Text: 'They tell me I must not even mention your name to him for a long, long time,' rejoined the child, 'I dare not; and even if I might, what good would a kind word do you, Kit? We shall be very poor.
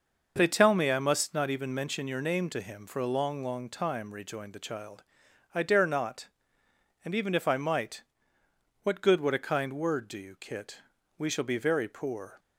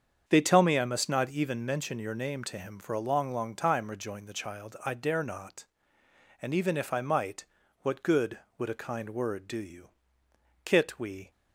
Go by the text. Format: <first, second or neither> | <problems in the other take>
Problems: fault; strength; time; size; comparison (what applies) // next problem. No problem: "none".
first | starts louder than the rest; strong; until 1.2 s; 7.5 dB // stops before "shall be very poor"; at 11.3 s